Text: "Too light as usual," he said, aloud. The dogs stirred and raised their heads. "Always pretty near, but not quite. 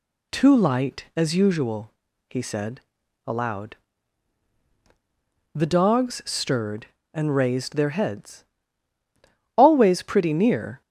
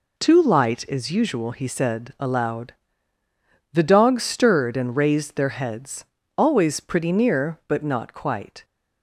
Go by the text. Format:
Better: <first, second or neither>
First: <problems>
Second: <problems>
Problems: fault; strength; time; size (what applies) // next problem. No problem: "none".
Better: second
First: stops before "but not quite"; at 10.8 s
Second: none